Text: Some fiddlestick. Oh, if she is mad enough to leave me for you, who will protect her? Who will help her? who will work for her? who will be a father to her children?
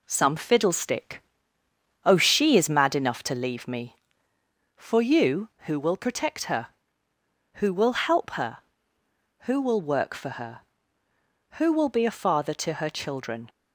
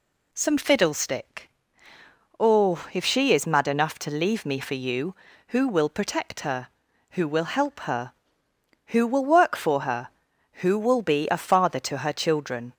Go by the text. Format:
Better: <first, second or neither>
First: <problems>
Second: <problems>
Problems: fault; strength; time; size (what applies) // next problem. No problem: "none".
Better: second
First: skips "if"; at 2.1 s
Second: none